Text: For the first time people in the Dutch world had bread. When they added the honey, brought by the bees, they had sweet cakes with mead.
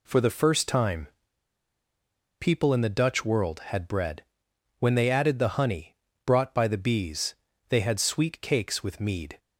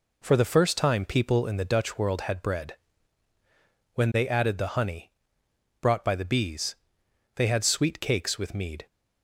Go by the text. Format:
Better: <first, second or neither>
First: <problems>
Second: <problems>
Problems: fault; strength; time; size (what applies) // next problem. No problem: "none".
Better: second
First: pauses between "time" and "people"; strong; at 1.0 s; 1.3 s long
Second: none